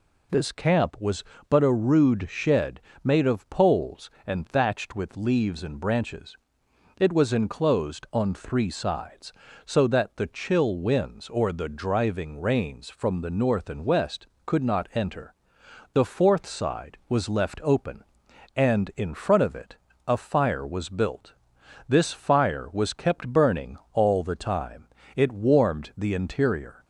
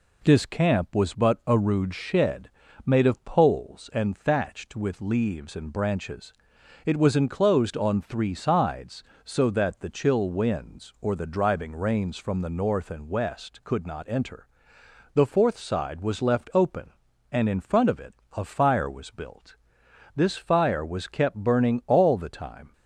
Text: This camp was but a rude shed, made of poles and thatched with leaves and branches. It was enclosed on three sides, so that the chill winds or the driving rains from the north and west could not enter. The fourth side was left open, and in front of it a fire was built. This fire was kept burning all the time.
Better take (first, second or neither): second